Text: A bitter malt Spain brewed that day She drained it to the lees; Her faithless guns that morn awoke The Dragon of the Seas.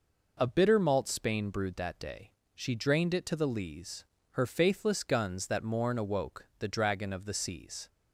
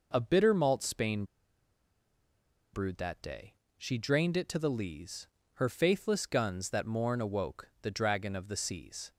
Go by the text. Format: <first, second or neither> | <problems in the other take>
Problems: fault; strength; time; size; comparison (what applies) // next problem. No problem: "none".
first | pauses between "Spain" and "brewed"; strong; at 1.2 s; 1.4 s long // pauses between "day" and "She"; slight; at 3.5 s; 0.22 s long; slight in the first